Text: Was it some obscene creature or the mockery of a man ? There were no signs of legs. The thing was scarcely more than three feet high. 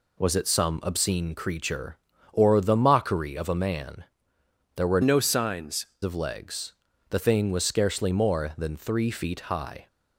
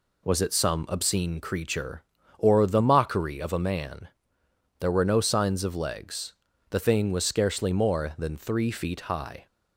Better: second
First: changes voice from "no" to "signs"; from 5.0 to 5.8 s; 0.8 s long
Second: none

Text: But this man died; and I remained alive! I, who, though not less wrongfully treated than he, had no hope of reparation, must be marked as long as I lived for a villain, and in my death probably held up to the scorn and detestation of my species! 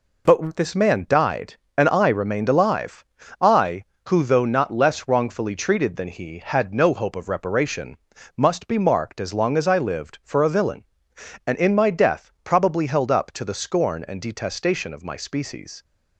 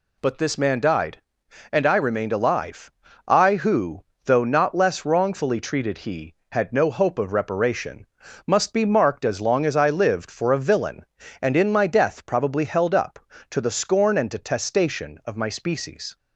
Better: first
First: none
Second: skips "than"; at 5.9 s

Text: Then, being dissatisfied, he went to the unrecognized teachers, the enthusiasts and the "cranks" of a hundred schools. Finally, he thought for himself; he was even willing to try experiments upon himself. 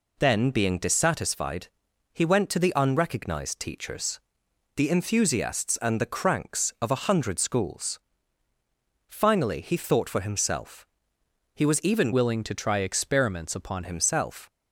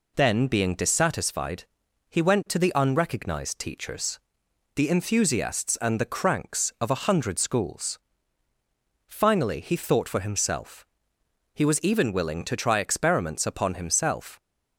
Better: second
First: changes voice from "willing" to "upon"; from 12.1 to 13.8 s; 1.7 s long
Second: none

